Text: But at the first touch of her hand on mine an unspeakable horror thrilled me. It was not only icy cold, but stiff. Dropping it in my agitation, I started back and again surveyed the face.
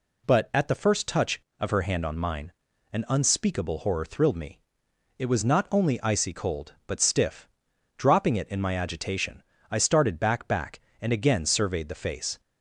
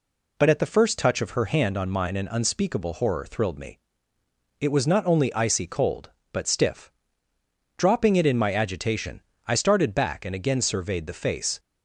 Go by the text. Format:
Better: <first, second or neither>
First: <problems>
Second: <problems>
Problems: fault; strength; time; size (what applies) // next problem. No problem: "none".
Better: second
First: pauses between "mine" and "an"; at 2.5 s; 0.42 s long // says "back" twice; at 10.4 s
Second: none